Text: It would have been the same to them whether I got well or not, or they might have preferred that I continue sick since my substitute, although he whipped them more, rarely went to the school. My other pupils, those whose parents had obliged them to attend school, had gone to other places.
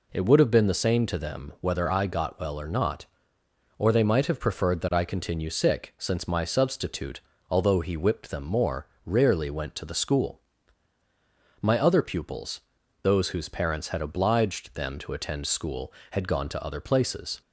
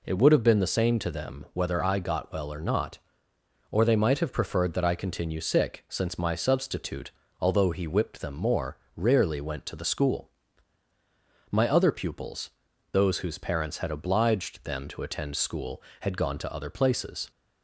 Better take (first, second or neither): neither